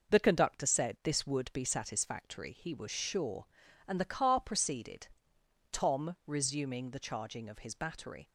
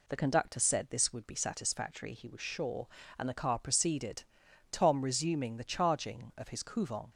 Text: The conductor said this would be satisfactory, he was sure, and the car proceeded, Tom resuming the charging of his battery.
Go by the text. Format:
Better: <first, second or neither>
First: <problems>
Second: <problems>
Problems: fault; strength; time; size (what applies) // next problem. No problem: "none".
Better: first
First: none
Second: says "couvent" for "battery"; at 6.6 s